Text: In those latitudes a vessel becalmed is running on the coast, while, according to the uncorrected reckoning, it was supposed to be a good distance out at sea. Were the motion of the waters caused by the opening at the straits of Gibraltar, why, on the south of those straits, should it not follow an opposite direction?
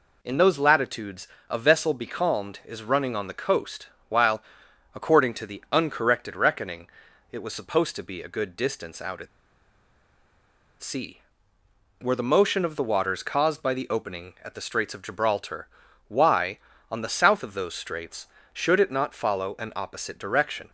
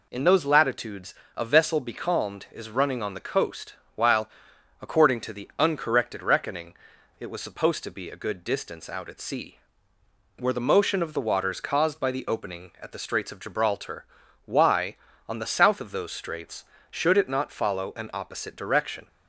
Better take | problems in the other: second | pauses between "latitudes" and "a"; slight; at 1.2 s; 0.22 s long; slight in the second // pauses between "at" and "sea"; strong; at 9.2 s; 1.5 s long

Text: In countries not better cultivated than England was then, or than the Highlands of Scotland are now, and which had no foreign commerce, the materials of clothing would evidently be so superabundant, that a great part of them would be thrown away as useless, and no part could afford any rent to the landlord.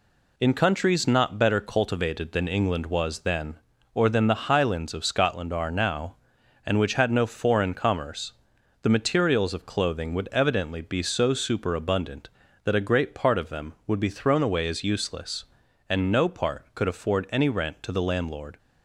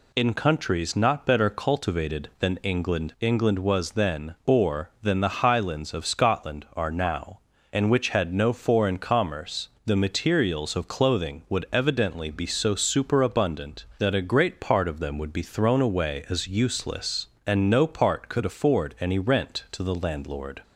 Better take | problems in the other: first | says "England" twice; at 3.1 s

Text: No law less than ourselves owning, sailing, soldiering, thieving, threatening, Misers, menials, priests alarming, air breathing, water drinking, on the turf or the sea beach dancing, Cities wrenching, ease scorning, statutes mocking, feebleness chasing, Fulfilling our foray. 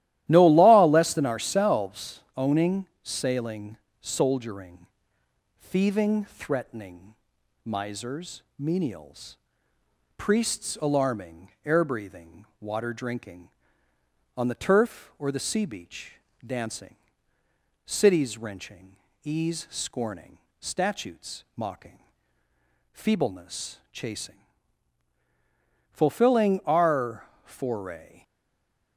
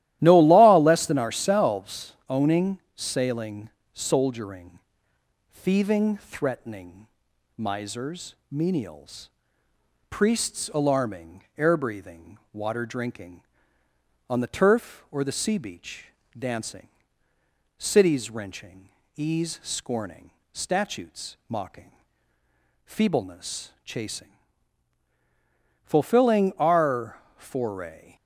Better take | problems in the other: second | starts louder than the rest; strong; until 1.2 s; 14 dB; strong in the second // pauses between "beach" and "dancing"; slight; at 16.1 s; 0.32 s long; slight in the second // pauses between "our" and "foray"; slight; at 27.2 s; 0.18 s long; slight in the second // stays silent after the last word; slight; from 28.2 s on; 0.7 s long

